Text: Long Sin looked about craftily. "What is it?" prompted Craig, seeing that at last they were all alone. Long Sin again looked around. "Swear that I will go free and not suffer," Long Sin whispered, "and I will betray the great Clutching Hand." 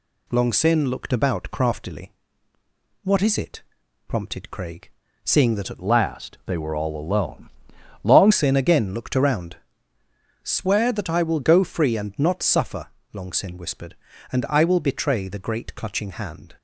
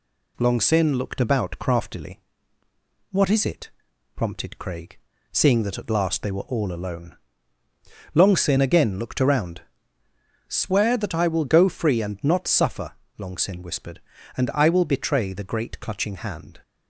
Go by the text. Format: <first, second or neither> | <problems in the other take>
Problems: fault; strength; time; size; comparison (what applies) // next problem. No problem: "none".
second | changes voice from "last" to "Long"; from 5.8 to 8.3 s; 2.5 s long